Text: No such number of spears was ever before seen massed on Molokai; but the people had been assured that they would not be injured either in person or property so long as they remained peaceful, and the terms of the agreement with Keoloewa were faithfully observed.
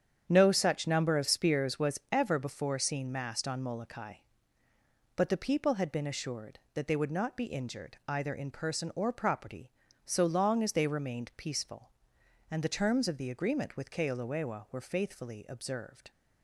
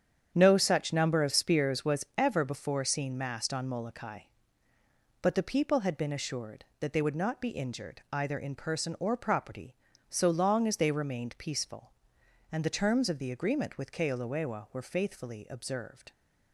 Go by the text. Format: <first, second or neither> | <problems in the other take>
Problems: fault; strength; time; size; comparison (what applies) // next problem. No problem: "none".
neither | starts louder than the rest; strong; the same in both